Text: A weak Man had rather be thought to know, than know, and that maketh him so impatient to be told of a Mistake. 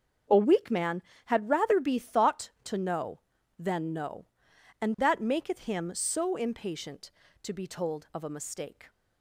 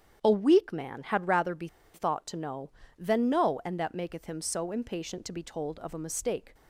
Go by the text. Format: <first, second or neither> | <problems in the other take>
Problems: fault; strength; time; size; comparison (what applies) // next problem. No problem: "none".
first | starts louder than the rest; strong; until 1.2 s; 8.5 dB; also in the first // pauses between "be" and "thought"; slight; at 1.6 s; 0.26 s long